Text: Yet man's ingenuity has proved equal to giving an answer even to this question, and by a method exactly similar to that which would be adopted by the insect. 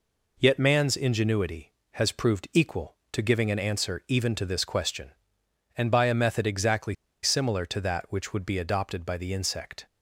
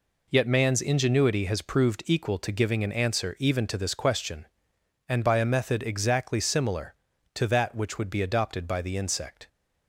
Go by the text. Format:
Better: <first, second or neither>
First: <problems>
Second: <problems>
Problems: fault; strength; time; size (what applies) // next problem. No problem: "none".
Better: second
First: pauses between "exactly" and "similar"; slight; at 6.9 s; 0.29 s long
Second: none